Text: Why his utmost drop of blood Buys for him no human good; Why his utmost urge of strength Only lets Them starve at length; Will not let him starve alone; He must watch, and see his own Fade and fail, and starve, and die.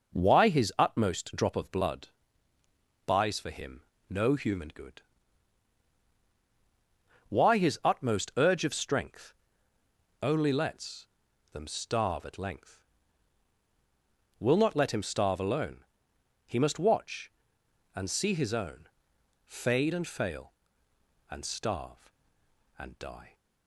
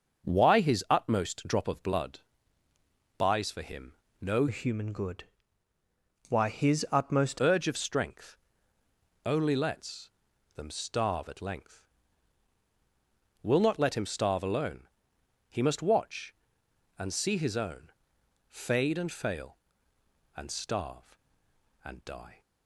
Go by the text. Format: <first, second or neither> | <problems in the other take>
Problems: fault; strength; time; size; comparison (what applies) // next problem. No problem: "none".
first | starts louder than the rest; until 1.3 s; 6.5 dB // pauses between "blood" and "Buys"; noticeable; at 2.2 s; 0.98 s long; noticeable in the first // pauses between "him" and "no"; slight; at 3.9 s; 0.30 s long; slight in the first // changes voice from "human" to "utmost"; from 4.4 to 7.3 s; 2.9 s long // pauses between "strength" and "Only"; noticeable; at 8.3 s; 0.88 s long; noticeable in the first // pauses between "lets" and "Them"; noticeable; at 10.1 s; 0.46 s long; noticeable in the first // pauses between "own" and "Fade"; noticeable; at 17.9 s; 0.58 s long; noticeable in the first